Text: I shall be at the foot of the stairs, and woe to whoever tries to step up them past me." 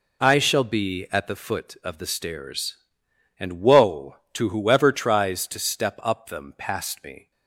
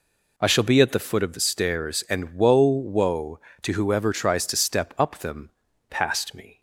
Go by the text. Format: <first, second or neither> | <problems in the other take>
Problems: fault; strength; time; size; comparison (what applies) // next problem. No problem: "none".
first | says "woe" twice; at 2.6 s // pauses between "them" and "past"; at 5.4 s; 0.40 s long